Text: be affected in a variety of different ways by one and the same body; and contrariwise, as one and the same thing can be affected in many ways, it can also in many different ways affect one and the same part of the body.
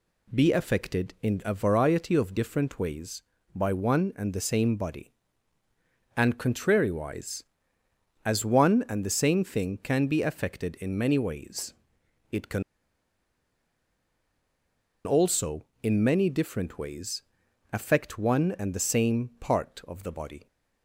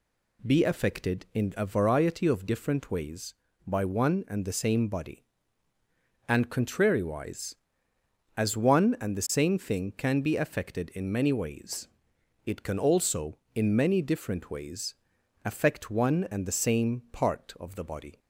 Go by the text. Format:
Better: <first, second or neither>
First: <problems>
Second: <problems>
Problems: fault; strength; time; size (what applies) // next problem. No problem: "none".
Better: second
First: pauses between "can" and "also"; strong; at 12.6 s; 2.4 s long // pauses between "ways" and "affect"; noticeable; at 17.2 s; 0.50 s long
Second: pauses between "ways" and "affect"; noticeable; at 14.9 s; 0.50 s long